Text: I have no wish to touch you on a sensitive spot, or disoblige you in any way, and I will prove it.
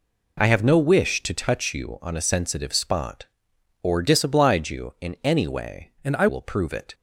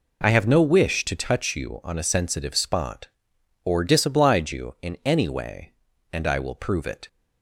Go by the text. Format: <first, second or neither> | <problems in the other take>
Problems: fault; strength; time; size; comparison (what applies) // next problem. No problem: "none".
second | changes voice from "and" to "I"; from 6.0 to 6.2 s; 0.2 s long